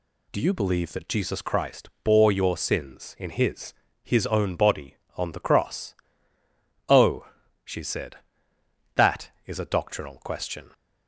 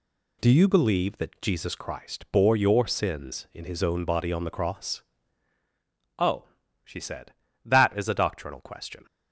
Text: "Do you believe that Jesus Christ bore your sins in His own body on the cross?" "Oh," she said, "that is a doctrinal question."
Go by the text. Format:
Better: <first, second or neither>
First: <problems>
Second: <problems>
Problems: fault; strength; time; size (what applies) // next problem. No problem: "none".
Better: second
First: says "His" twice; at 4.0 s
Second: none